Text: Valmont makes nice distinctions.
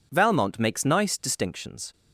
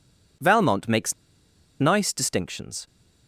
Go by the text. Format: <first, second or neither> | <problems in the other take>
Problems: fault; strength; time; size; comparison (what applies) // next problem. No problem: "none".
first | pauses between "makes" and "nice"; noticeable; at 1.1 s; 0.66 s long